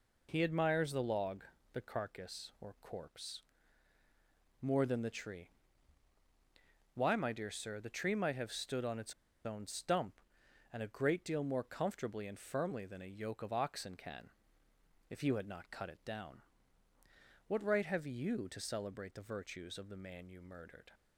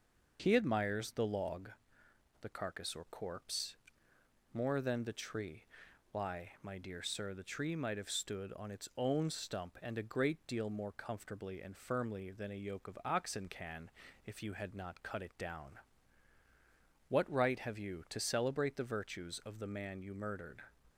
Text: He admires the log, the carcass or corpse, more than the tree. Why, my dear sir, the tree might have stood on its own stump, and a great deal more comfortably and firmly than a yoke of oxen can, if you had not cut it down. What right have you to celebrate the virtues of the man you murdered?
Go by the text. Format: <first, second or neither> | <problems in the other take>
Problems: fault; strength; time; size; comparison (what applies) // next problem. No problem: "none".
second | pauses between "its" and "own"; slight; at 9.1 s; 0.33 s long